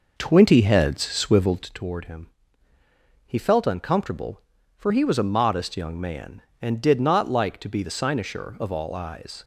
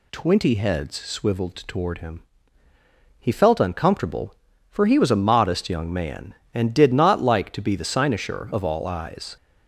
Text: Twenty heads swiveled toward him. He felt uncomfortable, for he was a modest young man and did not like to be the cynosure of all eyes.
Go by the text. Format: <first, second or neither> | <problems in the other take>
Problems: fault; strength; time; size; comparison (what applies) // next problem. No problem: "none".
second | starts louder than the rest; noticeable; until 1.7 s; 5 dB